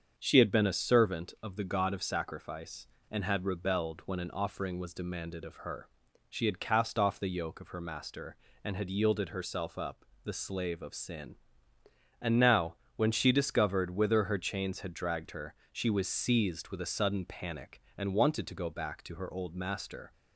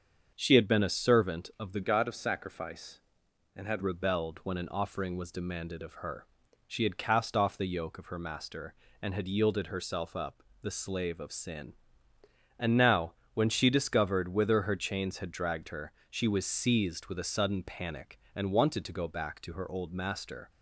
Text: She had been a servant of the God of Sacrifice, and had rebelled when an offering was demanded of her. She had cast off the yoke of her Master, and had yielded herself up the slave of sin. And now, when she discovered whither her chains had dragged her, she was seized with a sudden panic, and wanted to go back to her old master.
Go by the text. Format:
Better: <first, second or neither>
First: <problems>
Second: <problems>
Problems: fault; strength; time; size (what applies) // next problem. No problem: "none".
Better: first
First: starts louder than the rest; until 1.1 s; 7 dB // pauses between "up" and "the"; slight; at 10.0 s; 0.20 s long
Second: starts louder than the rest; until 1.3 s; 7 dB // changes voice from "God" to "had"; from 1.8 to 3.8 s; 2.0 s long // pauses between "up" and "the"; slight; at 10.4 s; 0.20 s long